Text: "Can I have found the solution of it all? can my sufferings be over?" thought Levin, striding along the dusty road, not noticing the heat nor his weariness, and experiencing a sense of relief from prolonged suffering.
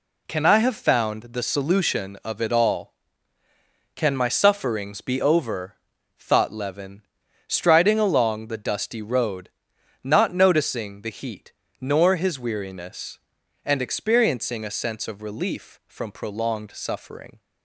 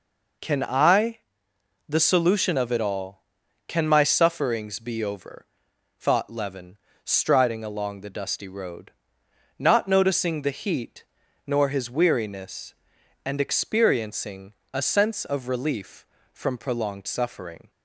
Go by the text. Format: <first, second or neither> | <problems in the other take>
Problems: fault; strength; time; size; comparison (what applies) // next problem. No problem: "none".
first | skips "have found"; at 1.5 s // pauses between "heat" and "nor"; at 11.0 s; 0.42 s long; slight in the first // pauses between "experiencing" and "a"; slight; at 14.5 s; 0.16 s long